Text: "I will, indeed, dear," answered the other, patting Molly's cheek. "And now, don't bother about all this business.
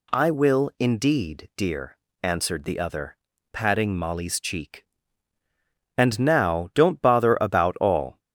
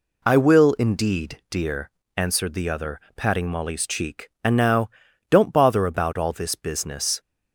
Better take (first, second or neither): second